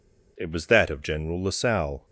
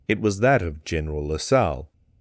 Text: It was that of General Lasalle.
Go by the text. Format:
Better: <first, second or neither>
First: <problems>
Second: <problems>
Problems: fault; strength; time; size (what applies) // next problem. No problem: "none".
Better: neither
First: none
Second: none